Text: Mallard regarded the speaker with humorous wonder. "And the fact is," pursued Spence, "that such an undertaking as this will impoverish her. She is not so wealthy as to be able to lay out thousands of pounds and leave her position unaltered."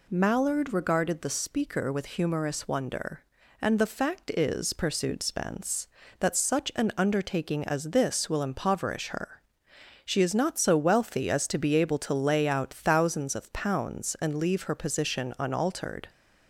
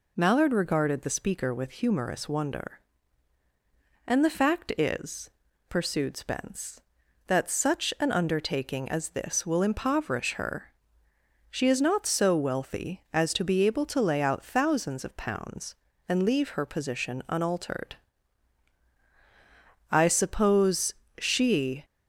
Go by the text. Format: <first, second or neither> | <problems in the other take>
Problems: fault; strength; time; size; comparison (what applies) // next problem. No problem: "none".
first | goes on to say "I suppose she"; strong; from 19.9 s on; 1.9 s long